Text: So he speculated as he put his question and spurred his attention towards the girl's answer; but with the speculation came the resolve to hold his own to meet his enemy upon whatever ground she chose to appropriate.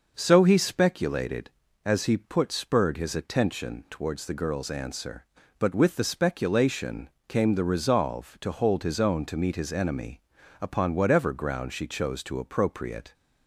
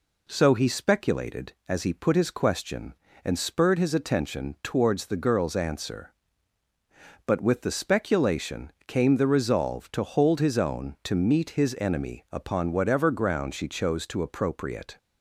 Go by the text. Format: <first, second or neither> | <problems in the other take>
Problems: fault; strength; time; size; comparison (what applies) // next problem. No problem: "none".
second | skips "his question and"; at 2.5 s // pauses between "speculation" and "came"; slight; at 7.0 s; 0.18 s long; slight in the second // pauses between "enemy" and "upon"; at 10.2 s; 0.40 s long